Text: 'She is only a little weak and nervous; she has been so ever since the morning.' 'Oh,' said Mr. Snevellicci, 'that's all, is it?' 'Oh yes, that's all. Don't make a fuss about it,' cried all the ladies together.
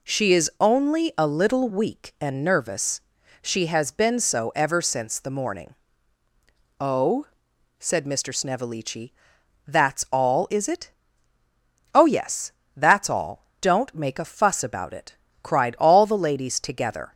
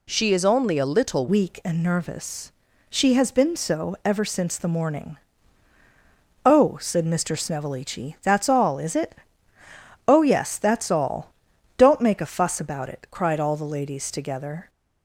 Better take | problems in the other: first | changes voice at "weak"; from 1.2 s on; 13.4 s long

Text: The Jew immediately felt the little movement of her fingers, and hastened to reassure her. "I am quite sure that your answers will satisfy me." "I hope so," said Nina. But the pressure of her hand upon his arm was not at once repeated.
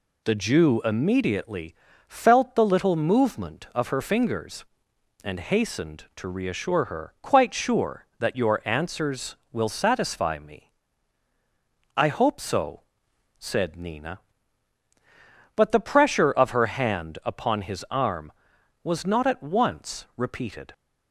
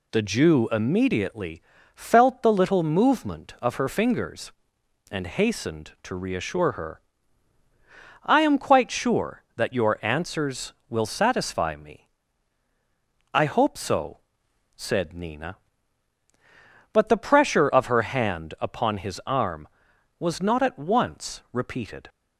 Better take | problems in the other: second | pauses between "immediately" and "felt"; slight; at 1.7 s; 0.32 s long; slight in the second // skips "I am"; at 7.1 s

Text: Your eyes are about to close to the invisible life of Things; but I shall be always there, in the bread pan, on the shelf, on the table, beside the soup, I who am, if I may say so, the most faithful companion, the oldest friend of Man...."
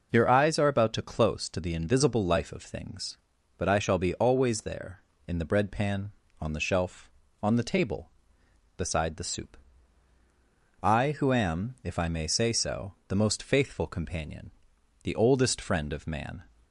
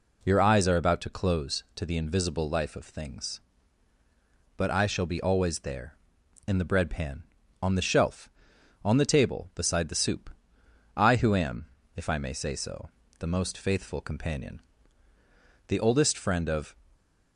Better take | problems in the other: first | stops before "Man"; at 16.9 s

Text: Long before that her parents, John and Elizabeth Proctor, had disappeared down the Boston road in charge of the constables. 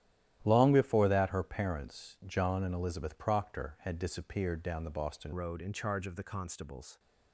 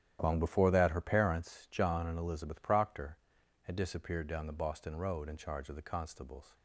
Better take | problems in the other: second | starts louder than the rest; strong; until 1.4 s; 12.5 dB; strong in the second // changes voice at "road"; from 5.3 s on; 1.6 s long

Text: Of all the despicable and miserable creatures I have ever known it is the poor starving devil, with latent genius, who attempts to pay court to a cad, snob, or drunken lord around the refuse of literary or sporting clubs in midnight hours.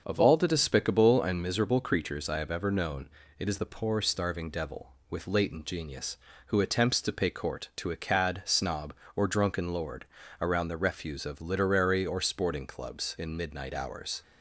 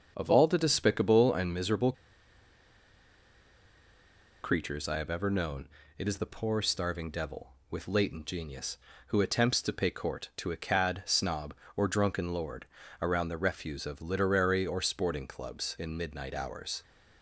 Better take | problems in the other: first | starts louder than the rest; until 1.1 s; 6.5 dB; also in the first // pauses between "miserable" and "creatures"; strong; at 1.9 s; 2.5 s long // pauses between "known" and "it"; slight; at 5.6 s; 0.28 s long; slight in the first // pauses between "lord" and "around"; slight; at 12.6 s; 0.34 s long; slight in the first

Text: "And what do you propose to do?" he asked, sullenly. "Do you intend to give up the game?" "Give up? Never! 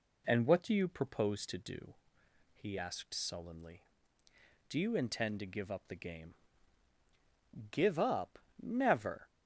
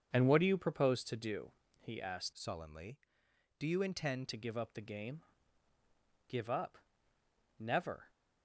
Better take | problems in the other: first | starts louder than the rest; until 1.1 s; 7 dB // changes voice from "sullenly" to "intend"; from 2.3 to 4.2 s; 1.9 s long

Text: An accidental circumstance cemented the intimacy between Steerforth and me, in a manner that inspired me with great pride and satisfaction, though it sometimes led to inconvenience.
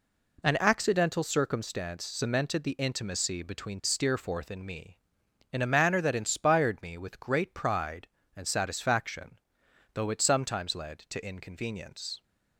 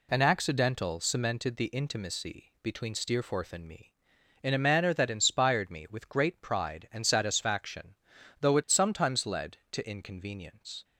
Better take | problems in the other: first | skips "circumstance"; at 0.9 s

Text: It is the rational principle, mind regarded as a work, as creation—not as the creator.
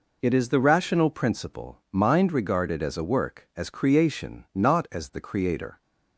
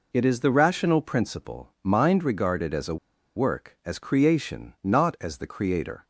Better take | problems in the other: first | pauses between "a" and "work"; at 2.9 s; 0.40 s long

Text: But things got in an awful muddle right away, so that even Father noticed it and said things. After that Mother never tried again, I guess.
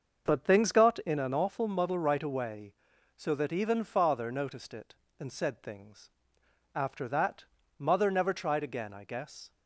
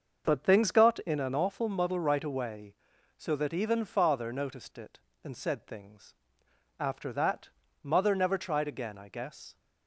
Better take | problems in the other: neither | starts louder than the rest; the same in both // pauses between "that" and "Mother"; slight; the same in both

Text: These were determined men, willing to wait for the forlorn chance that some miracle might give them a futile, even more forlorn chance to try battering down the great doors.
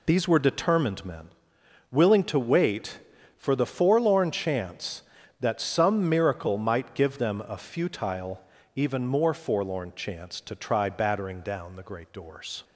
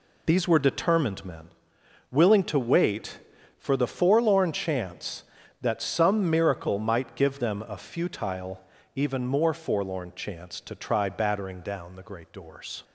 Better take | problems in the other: neither | none

